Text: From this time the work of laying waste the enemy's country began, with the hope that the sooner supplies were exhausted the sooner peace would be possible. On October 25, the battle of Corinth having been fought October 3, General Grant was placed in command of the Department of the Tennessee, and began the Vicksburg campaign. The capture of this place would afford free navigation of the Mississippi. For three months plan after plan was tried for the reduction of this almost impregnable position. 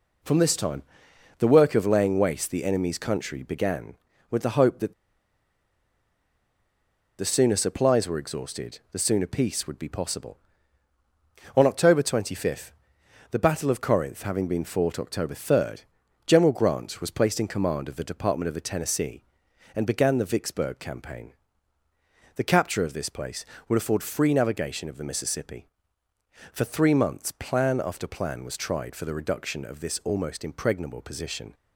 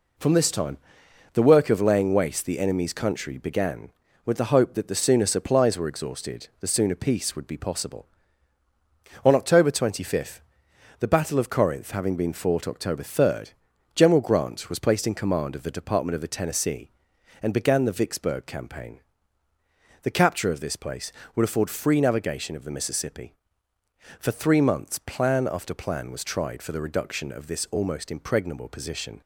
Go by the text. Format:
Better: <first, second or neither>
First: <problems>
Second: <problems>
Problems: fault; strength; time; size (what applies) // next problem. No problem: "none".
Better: second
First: pauses between "time" and "the"; noticeable; at 0.8 s; 0.56 s long // pauses between "that" and "the"; strong; at 4.9 s; 2.2 s long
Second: pauses between "time" and "the"; noticeable; at 0.7 s; 0.56 s long